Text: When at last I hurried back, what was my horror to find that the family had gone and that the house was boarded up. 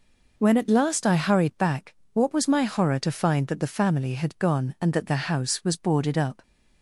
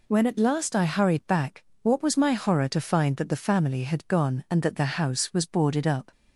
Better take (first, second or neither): second